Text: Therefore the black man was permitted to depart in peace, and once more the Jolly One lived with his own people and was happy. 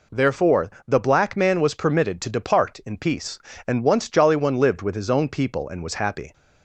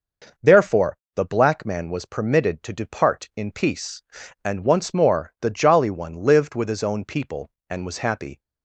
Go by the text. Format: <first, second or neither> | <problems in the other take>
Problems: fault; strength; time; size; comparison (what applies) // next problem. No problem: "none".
second | pauses between "Therefore" and "the"; slight; at 0.7 s; 0.16 s long; slight in the second // skips "more the"; at 4.0 s